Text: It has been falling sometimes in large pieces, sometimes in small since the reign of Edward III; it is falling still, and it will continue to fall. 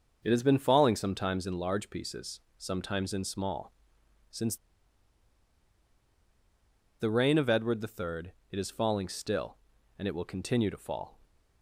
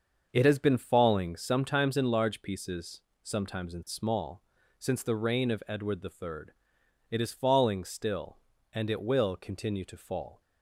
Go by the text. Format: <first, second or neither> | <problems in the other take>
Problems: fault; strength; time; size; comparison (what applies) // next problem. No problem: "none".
second | starts louder than the rest; until 1.2 s; 6.5 dB; also in the second // pauses between "small" and "since"; noticeable; at 3.7 s; 0.58 s long; slight in the second // pauses between "since" and "the"; strong; at 4.5 s; 2.4 s long